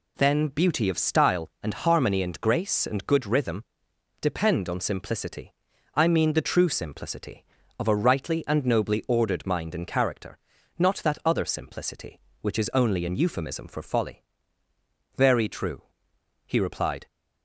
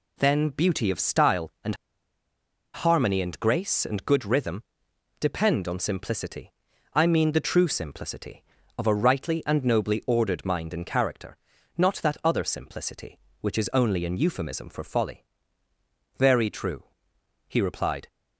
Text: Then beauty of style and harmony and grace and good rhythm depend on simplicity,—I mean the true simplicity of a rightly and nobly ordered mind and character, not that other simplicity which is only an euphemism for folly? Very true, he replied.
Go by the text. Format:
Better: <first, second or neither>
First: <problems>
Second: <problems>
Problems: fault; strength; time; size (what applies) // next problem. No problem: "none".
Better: first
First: pauses between "rhythm" and "depend"; noticeable; at 3.6 s; 0.58 s long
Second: pauses between "and" and "harmony"; at 1.7 s; 0.99 s long // pauses between "rhythm" and "depend"; noticeable; at 4.6 s; 0.58 s long